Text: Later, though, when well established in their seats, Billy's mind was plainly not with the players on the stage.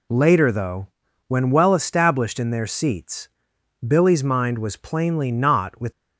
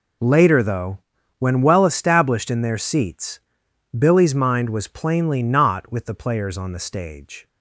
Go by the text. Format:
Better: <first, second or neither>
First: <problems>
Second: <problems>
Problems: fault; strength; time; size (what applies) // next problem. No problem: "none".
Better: second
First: stops before "the players on the stage"; at 5.9 s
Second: none